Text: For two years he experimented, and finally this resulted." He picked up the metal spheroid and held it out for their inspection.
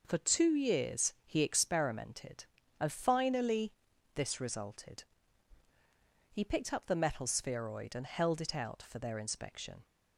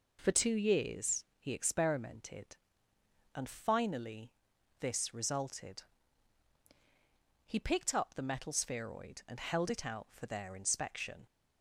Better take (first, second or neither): neither